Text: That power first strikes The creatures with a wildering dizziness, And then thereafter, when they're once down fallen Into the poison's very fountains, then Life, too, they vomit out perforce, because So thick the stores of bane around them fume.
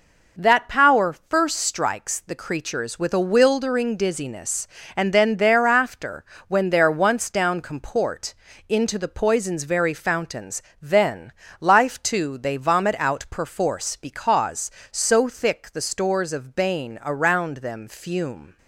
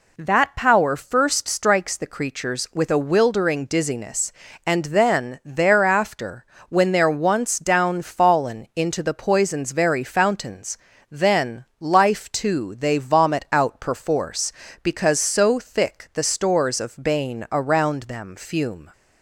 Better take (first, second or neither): second